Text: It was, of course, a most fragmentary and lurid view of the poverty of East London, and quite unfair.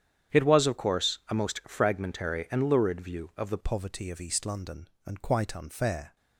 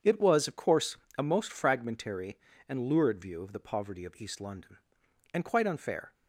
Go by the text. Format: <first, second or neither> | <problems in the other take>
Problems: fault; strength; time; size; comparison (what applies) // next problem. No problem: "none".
second | starts louder than the rest; strong; until 1.4 s; 9.5 dB; strong in the second // changes voice at "poverty"; from 3.6 s on; 2.5 s long